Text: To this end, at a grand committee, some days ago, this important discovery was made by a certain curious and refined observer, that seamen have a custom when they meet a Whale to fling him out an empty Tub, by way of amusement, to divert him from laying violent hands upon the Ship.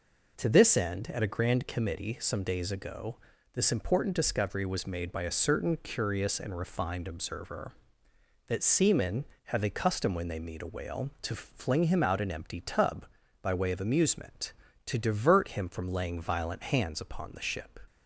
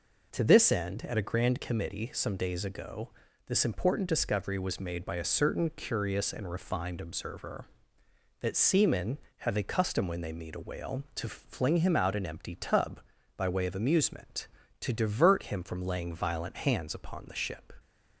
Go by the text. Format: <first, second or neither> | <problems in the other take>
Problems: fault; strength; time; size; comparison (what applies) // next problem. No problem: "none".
neither | none